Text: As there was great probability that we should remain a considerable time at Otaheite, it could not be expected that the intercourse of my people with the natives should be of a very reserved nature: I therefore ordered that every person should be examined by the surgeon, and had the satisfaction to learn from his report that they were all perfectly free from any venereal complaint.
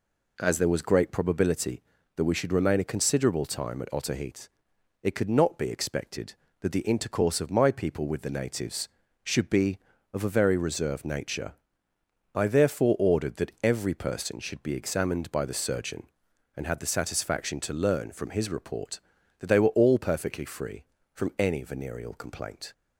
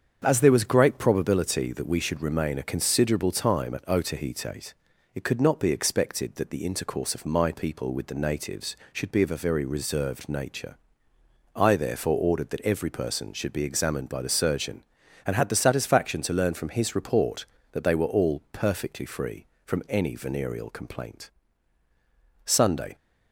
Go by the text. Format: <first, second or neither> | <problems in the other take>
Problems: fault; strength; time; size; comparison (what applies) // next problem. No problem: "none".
first | starts louder than the rest; strong; until 1.2 s; 7.5 dB // goes on to say "Sunday"; from 22.4 s on; 0.50 s long